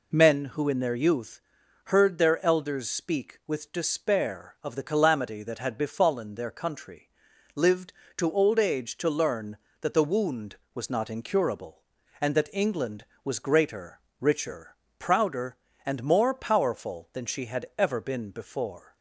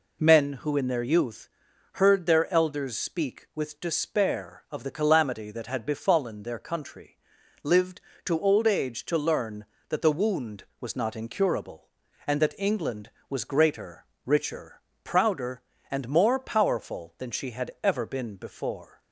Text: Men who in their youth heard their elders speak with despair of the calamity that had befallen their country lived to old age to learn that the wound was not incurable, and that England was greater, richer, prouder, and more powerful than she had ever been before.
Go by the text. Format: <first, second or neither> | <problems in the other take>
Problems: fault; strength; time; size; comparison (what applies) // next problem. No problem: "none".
neither | pauses between "youth" and "heard"; noticeable; the same in both // pauses between "country" and "lived"; noticeable; the same in both